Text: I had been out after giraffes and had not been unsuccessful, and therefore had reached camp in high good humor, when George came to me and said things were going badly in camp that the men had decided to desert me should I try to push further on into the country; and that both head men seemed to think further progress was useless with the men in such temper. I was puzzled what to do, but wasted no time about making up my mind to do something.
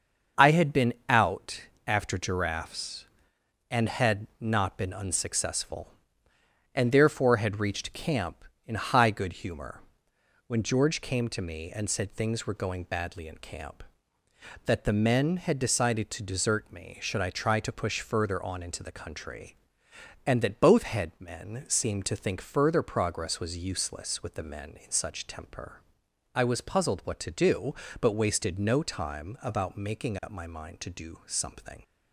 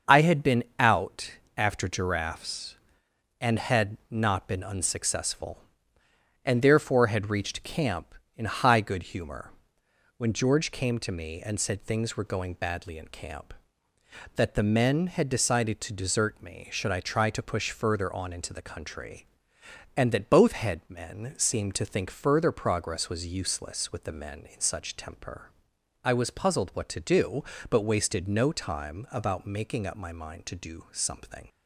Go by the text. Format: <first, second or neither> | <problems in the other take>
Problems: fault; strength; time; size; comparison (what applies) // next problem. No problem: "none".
neither | starts louder than the rest; the same in both // pauses between "out" and "after"; slight; the same in both